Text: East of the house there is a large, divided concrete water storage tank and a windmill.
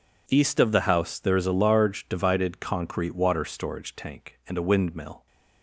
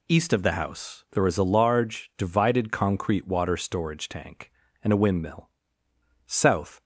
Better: first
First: none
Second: goes on to say "South"; from 6.2 s on; 0.56 s long

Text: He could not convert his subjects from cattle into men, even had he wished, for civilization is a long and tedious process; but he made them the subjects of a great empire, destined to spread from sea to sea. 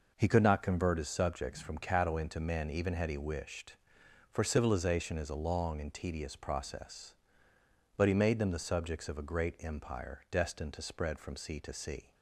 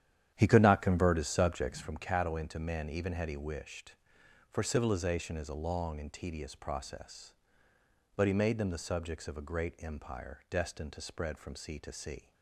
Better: first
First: none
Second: starts louder than the rest; strong; until 2.0 s; 10 dB

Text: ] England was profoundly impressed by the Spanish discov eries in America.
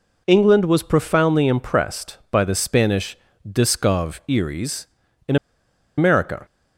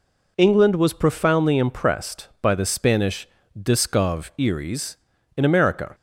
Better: second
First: pauses between "Spanish" and "discov"; slight; at 3.1 s; 0.28 s long // pauses between "in" and "America"; noticeable; at 5.3 s; 0.61 s long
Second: pauses between "Spanish" and "discov"; slight; at 3.2 s; 0.28 s long

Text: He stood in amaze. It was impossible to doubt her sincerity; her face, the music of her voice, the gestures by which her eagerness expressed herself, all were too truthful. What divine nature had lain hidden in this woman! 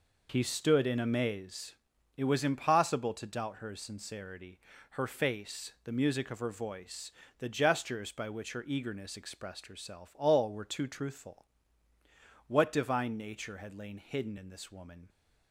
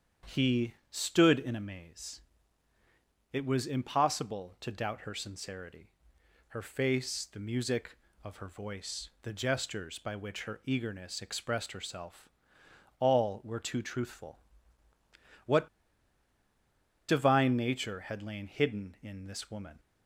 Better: first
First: none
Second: starts louder than the rest; strong; until 1.4 s; 8 dB // pauses between "He" and "stood"; slight; at 0.7 s; 0.16 s long // pauses between "What" and "divine"; strong; at 15.6 s; 1.4 s long

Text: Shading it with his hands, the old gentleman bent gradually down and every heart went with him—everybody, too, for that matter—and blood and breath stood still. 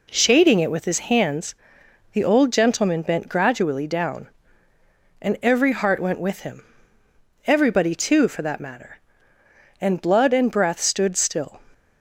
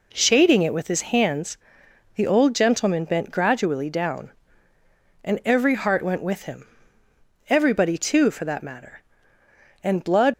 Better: first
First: none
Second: stops before "and breath stood still"; at 10.3 s

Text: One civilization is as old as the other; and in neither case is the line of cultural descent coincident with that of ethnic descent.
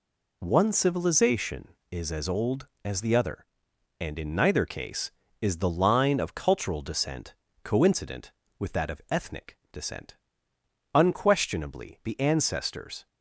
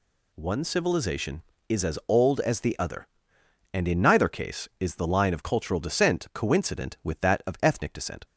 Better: second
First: pauses between "descent" and "coincident"; slight; at 7.3 s; 0.30 s long // pauses between "ethnic" and "descent"; slight; at 9.5 s; 0.18 s long // goes on to say "Unquestionably the ancestors"; strong; from 10.9 s on; 2.1 s long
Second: none

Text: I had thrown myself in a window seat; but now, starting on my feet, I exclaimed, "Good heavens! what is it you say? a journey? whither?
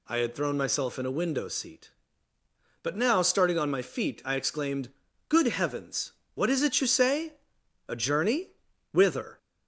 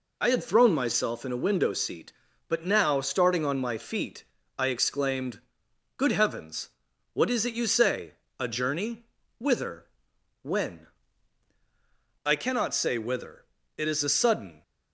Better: first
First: none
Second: goes on to say "when I cannot say whither It is a sudden"; strong; from 10.4 s on; 4.2 s long

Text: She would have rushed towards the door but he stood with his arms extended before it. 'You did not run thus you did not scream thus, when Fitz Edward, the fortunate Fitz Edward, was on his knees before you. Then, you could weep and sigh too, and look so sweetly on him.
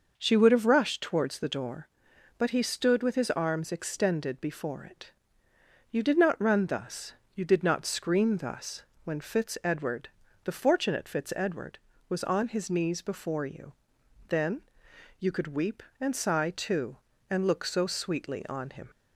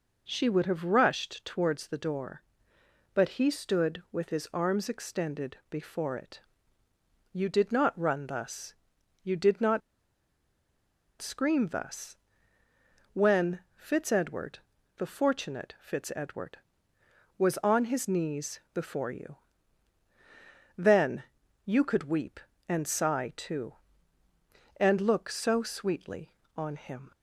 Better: first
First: pauses between "thus" and "you"; slight; at 7.1 s; 0.22 s long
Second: pauses between "thus" and "you"; noticeable; at 8.7 s; 0.48 s long // pauses between "not" and "scream"; strong; at 9.8 s; 1.4 s long // pauses between "when" and "Fitz"; slight; at 13.5 s; 0.16 s long

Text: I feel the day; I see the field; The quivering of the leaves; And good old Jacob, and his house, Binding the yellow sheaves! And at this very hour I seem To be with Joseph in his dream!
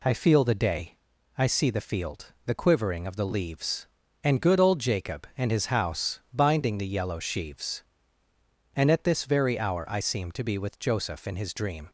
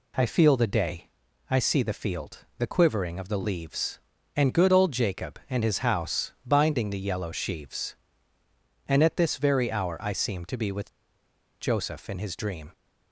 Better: first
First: none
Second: pauses between "with" and "Joseph"; noticeable; at 10.9 s; 0.68 s long

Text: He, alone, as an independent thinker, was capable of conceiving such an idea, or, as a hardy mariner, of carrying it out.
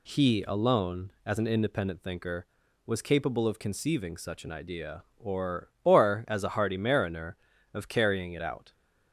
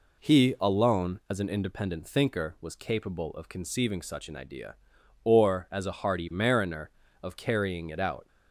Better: second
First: says "or" twice; at 5.8 s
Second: none

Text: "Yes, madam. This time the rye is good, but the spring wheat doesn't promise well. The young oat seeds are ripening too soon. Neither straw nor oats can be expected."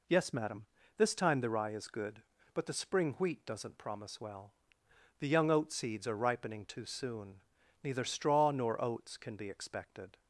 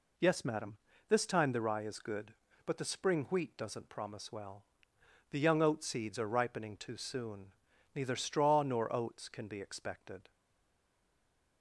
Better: first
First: none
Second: stays silent after the last word; noticeable; from 10.3 s on; 1.3 s long

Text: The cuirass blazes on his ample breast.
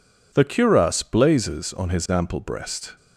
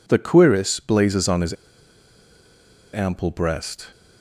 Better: first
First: none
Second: pauses between "his" and "ample"; strong; at 1.5 s; 1.4 s long

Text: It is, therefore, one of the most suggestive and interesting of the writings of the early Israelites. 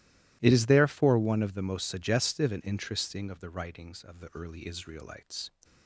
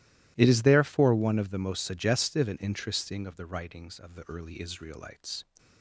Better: neither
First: starts louder than the rest; strong; until 1.4 s; 16 dB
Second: starts louder than the rest; strong; until 1.3 s; 16 dB

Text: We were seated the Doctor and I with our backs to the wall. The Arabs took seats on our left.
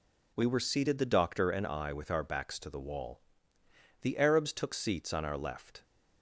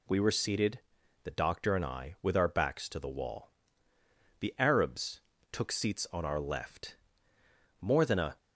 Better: first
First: none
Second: pauses between "seated" and "the"; at 0.7 s; 0.44 s long // pauses between "Arabs" and "took"; slight; at 5.1 s; 0.32 s long // goes on to say "More than a"; from 7.8 s on; 0.56 s long

